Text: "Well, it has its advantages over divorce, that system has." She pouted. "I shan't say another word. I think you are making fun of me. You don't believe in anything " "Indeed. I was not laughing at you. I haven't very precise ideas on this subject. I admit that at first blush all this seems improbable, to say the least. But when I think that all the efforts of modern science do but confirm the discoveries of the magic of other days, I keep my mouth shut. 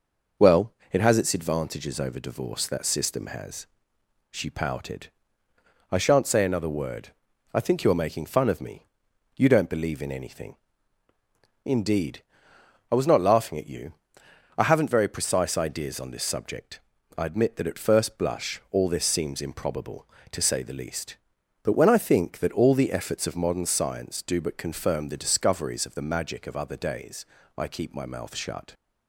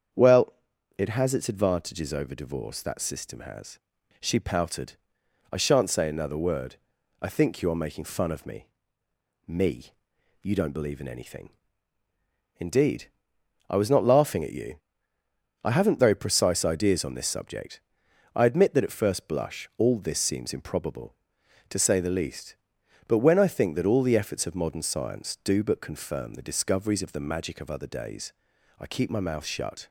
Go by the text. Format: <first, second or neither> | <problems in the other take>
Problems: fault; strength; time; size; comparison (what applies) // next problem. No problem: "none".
first | starts louder than the rest; strong; until 1.6 s; 7.5 dB // says "me" twice; at 9.4 s